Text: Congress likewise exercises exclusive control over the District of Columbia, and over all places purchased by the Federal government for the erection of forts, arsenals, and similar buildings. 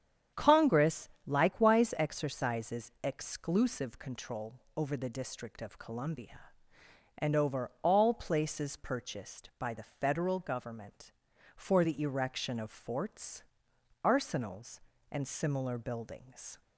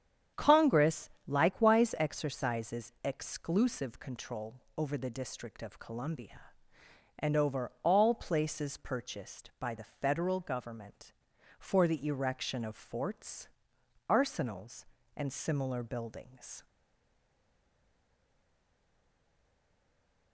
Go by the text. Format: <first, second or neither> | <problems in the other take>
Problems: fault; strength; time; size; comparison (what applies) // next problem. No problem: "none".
first | starts louder than the rest; strong; until 1.5 s; 8.5 dB; strong in the first // pauses between "Congress" and "likewise"; slight; at 1.0 s; 0.18 s long; slight in the first // pauses between "control" and "over"; slight; at 4.5 s; 0.20 s long; slight in the first // stays silent after the last word; strong; from 16.6 s on; 3.7 s long